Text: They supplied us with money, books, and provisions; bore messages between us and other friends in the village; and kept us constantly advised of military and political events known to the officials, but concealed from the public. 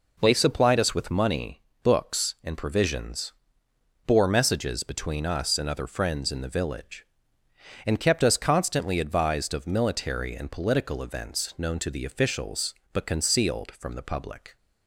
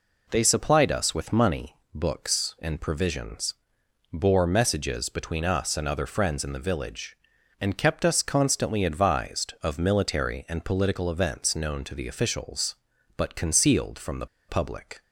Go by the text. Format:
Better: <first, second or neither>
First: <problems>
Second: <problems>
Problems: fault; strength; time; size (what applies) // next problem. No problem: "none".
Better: first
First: none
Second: pauses between "the" and "public"; slight; at 14.2 s; 0.22 s long